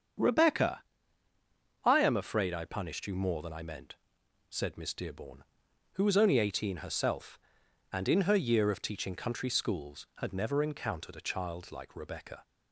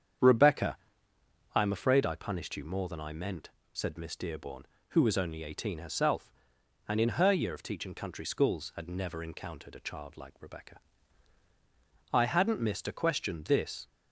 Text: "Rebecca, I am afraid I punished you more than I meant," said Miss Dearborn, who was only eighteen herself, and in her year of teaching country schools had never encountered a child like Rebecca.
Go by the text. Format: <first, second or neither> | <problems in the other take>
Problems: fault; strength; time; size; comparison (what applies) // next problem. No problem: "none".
first | starts louder than the rest; strong; until 1.9 s; 8 dB; strong in the first // goes on to say "I hadn't missed a question this"; strong; from 12.1 s on; 1.7 s long